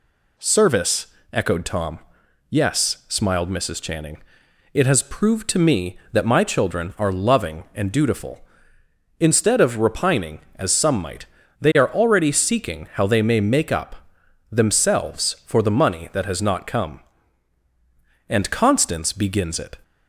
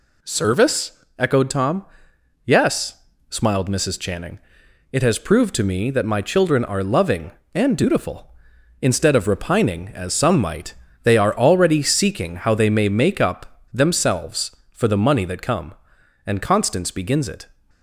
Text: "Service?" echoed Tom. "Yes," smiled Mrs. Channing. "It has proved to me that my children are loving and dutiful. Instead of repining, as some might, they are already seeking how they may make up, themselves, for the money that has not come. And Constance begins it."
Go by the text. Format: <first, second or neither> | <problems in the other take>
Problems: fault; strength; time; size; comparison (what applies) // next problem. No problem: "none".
first | skips "has not"; at 15.4 s